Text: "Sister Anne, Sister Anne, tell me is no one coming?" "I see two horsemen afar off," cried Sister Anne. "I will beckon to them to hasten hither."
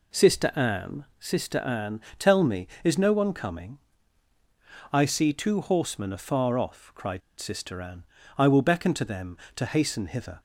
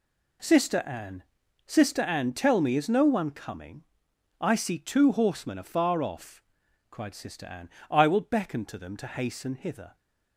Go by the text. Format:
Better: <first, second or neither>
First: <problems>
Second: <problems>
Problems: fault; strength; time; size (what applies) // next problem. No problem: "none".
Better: second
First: pauses between "cried" and "Sister"; slight; at 7.2 s; 0.19 s long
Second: none